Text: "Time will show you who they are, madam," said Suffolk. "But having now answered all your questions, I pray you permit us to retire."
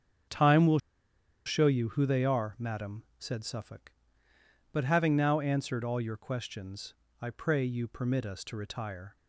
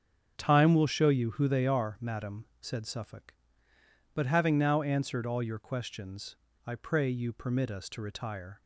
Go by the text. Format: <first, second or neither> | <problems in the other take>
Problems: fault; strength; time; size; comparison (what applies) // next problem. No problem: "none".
second | starts louder than the rest; strong; until 1.9 s; 8 dB; strong in the second // pauses between "will" and "show"; noticeable; at 0.7 s; 0.66 s long